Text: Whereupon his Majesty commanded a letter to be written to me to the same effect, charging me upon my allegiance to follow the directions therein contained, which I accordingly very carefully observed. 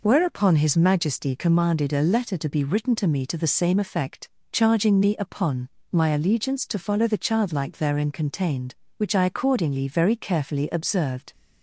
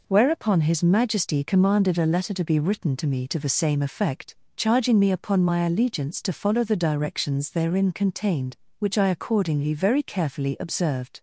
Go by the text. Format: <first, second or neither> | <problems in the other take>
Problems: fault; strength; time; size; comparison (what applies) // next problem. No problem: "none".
second | pauses between "upon" and "my"; slight; at 5.6 s; 0.24 s long // says "childlike" for "directions"; at 7.2 s